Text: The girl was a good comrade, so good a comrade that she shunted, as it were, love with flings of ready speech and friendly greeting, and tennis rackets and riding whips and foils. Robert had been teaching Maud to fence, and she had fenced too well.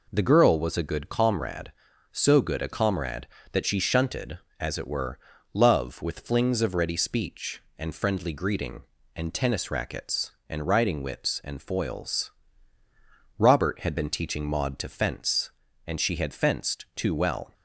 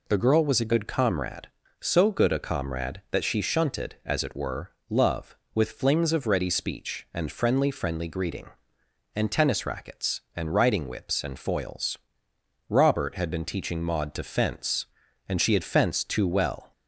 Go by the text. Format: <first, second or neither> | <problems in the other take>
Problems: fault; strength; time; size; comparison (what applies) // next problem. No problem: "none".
first | says "friendly" twice; at 7.6 s